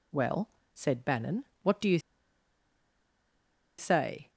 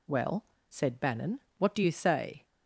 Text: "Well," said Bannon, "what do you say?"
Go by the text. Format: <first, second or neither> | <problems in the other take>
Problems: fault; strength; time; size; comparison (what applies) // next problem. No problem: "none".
second | pauses between "you" and "say"; strong; at 1.9 s; 1.7 s long